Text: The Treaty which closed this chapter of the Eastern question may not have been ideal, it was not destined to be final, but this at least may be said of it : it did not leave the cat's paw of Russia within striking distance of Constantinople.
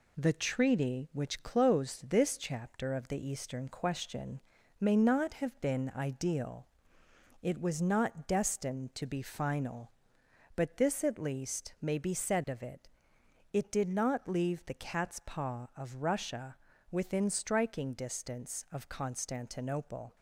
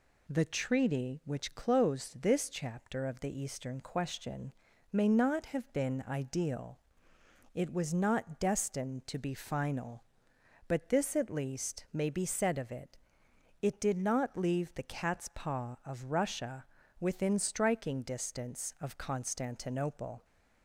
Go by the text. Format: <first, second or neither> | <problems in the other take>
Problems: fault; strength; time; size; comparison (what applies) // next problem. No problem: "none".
second | gets quieter; slight; throughout; 3 dB // pauses between "question" and "may"; at 4.4 s; 0.38 s long; also in the second // pauses between "Russia" and "within"; slight; at 16.5 s; 0.34 s long; slight in the second